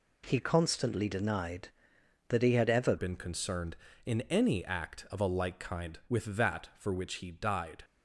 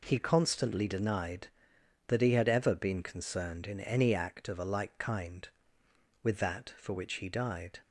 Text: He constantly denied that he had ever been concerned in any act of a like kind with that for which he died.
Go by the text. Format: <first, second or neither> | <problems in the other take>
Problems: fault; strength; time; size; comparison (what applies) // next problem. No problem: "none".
second | changes voice at "been"; from 2.9 s on; 4.9 s long